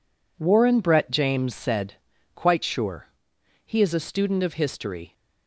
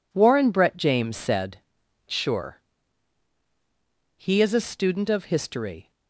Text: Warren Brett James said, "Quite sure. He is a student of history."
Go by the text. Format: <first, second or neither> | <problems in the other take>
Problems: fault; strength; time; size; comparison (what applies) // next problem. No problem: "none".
first | skips "Quite"; at 1.8 s